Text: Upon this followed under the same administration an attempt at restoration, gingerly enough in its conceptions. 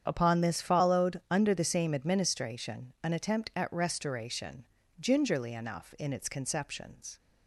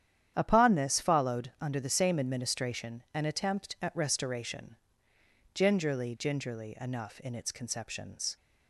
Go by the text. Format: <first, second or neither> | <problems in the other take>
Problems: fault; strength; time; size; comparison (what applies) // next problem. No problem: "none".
first | starts louder than the rest; strong; until 1.3 s; 10 dB; strong in the first // says "gingerly" twice; at 6.1 s